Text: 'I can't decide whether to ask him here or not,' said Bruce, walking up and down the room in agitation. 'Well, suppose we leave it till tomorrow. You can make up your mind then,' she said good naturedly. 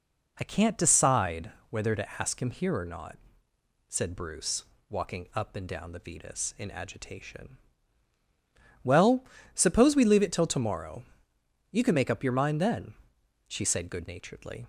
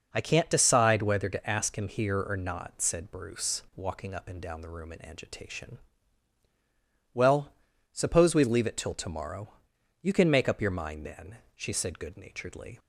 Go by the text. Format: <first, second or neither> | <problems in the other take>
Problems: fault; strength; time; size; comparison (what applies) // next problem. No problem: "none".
second | pauses between "decide" and "whether"; slight; at 1.5 s; 0.18 s long // says "vetus" for "room"; at 5.9 s